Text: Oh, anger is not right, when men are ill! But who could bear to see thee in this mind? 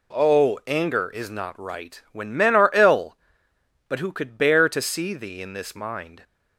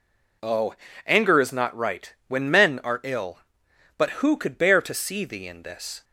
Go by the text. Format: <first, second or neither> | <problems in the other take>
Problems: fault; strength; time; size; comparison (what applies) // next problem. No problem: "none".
first | stops before "mind"; at 6.0 s